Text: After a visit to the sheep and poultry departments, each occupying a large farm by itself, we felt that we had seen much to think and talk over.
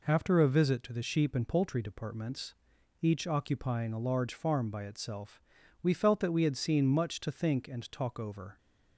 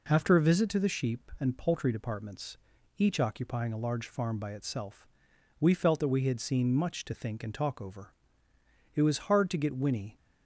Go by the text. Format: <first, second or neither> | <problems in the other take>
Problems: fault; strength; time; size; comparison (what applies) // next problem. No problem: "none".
first | goes on to say "It was hard to get Winnie"; noticeable; from 8.9 s on; 1.2 s long